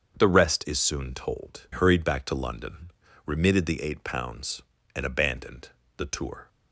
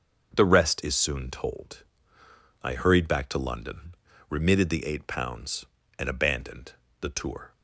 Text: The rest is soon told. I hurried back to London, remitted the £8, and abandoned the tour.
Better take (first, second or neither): second